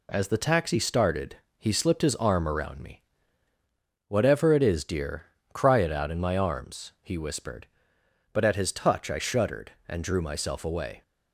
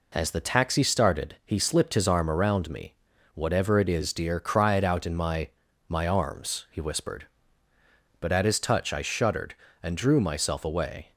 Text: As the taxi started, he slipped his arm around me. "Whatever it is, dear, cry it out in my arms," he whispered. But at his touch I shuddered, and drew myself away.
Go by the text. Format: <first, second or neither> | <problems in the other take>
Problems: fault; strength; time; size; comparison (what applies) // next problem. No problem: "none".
first | says "my" twice; at 5.8 s